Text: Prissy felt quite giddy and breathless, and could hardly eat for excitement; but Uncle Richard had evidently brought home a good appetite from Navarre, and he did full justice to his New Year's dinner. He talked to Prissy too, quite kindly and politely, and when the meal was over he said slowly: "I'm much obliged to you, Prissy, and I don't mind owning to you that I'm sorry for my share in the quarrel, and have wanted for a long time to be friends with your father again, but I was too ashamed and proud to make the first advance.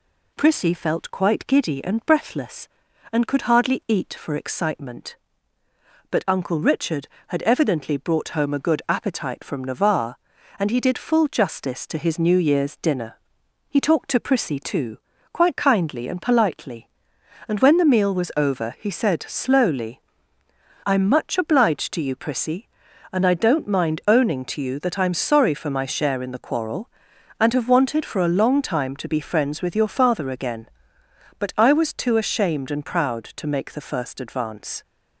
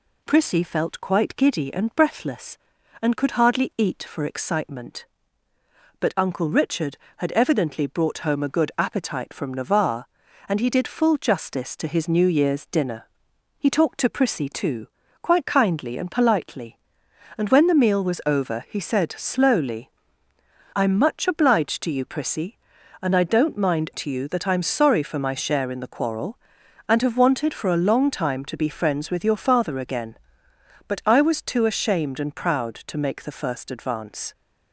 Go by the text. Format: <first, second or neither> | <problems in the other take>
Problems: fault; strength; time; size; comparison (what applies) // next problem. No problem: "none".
first | skips "owning"; at 23.9 s